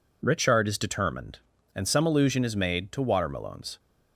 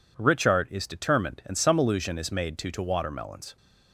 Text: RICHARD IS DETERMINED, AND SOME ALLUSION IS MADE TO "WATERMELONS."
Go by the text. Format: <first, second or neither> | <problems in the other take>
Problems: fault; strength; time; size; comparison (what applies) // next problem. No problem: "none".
first | says "TO" twice; at 2.7 s